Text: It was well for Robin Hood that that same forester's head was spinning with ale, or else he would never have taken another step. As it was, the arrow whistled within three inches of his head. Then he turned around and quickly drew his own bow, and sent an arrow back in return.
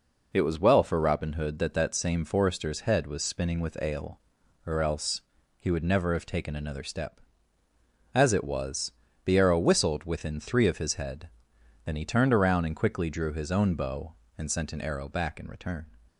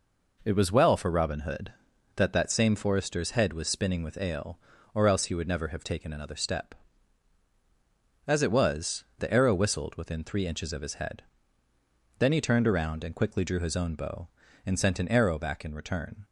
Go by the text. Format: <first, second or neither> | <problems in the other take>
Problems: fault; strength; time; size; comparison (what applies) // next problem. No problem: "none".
second | pauses between "else" and "he"; at 5.2 s; 0.38 s long // skips "inches"; at 10.6 s